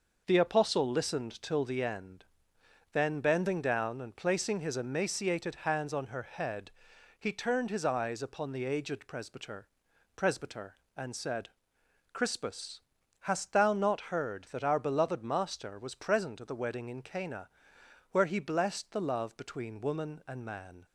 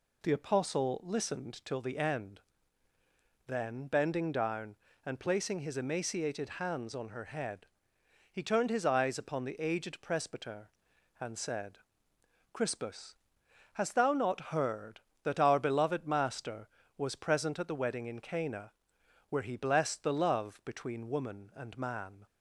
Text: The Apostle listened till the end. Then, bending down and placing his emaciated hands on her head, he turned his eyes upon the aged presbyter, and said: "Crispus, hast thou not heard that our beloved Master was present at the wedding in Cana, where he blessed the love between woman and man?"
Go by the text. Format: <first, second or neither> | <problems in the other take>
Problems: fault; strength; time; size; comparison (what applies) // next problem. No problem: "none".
second | says "presbyter" twice; at 10.1 s